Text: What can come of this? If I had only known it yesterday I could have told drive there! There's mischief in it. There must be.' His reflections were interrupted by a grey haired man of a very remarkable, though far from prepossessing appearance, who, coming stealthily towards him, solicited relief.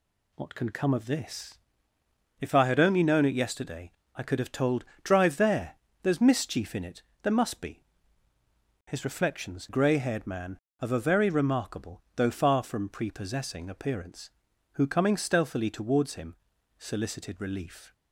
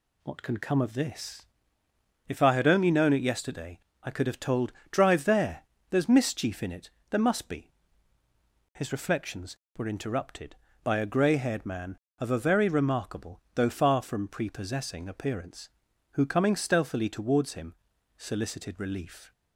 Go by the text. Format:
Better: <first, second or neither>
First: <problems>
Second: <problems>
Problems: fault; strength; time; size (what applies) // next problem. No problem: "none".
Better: second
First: pauses between "yesterday" and "I"; slight; at 3.9 s; 0.24 s long // pauses between "told" and "drive"; slight; at 4.8 s; 0.18 s long // skips "were interrupted by a"; at 9.6 s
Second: pauses between "yesterday" and "I"; slight; at 3.7 s; 0.24 s long // pauses between "told" and "drive"; slight; at 4.7 s; 0.18 s long